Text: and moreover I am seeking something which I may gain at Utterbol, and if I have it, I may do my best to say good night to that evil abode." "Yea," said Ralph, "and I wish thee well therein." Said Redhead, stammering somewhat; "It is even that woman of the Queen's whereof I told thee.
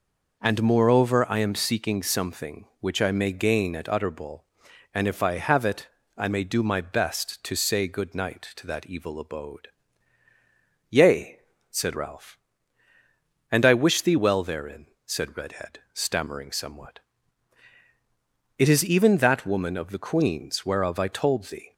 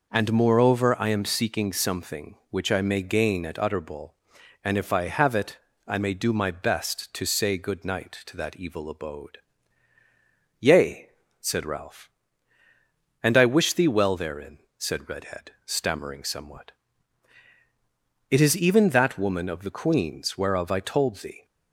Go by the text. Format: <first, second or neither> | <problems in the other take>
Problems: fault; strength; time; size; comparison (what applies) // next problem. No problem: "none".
neither | none